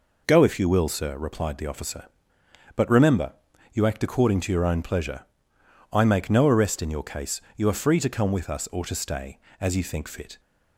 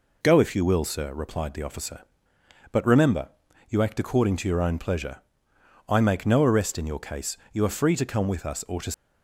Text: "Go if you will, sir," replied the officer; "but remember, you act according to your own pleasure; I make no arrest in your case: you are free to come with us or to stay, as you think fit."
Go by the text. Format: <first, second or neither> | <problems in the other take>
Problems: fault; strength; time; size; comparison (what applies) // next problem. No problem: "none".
first | stops before "stay as you think fit"; at 8.9 s